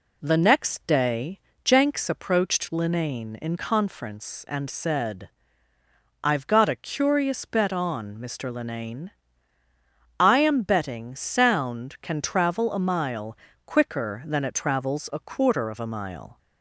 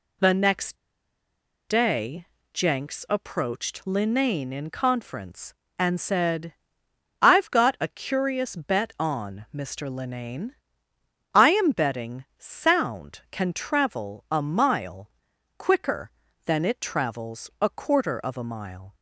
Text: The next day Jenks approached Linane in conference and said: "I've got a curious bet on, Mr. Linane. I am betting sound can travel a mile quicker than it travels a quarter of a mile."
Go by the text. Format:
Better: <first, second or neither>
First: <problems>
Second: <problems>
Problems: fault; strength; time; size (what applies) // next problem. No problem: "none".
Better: first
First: pauses between "day" and "Jenks"; slight; at 1.3 s; 0.26 s long // pauses between "mile" and "quicker"; slight; at 13.3 s; 0.30 s long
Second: pauses between "next" and "day"; noticeable; at 0.7 s; 0.93 s long // pauses between "day" and "Jenks"; slight; at 2.2 s; 0.26 s long // pauses between "mile" and "quicker"; noticeable; at 15.1 s; 0.48 s long